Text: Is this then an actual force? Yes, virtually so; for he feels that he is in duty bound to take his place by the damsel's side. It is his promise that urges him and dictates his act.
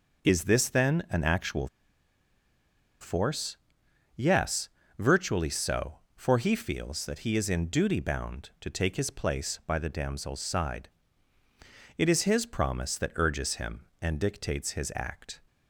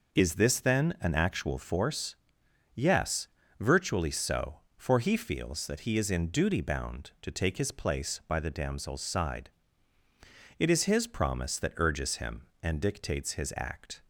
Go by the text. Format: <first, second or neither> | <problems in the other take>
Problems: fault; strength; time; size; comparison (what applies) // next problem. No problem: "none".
second | pauses between "actual" and "force"; strong; at 1.6 s; 1.3 s long